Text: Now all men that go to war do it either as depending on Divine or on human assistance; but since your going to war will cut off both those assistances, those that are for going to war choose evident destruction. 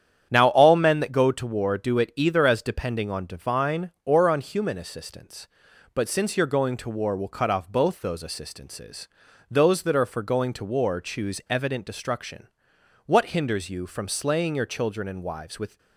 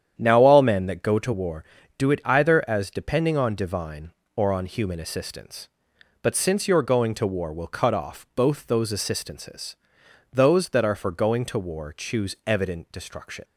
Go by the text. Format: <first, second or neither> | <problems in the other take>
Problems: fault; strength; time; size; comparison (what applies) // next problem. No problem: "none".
second | starts louder than the rest; strong; until 1.3 s; 9 dB; strong in the second // goes on to say "What hinders you from slaying your children and wives with"; strong; from 13.0 s on; 2.7 s long